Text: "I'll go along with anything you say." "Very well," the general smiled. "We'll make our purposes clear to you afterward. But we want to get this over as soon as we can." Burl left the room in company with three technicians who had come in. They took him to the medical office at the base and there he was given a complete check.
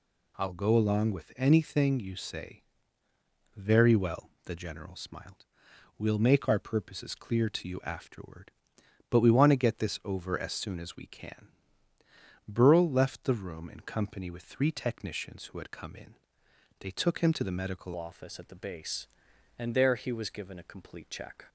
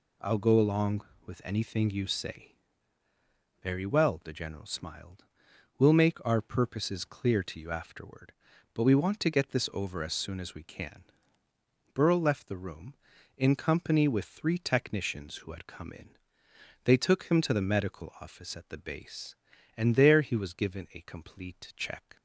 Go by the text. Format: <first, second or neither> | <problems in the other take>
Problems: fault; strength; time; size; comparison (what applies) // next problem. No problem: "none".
second | changes voice at "office"; from 17.9 s on; 3.5 s long